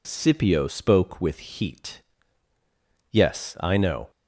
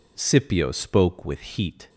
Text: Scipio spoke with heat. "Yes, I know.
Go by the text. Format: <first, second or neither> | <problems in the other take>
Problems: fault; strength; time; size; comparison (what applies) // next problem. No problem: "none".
first | stops before "Yes I know"; at 1.8 s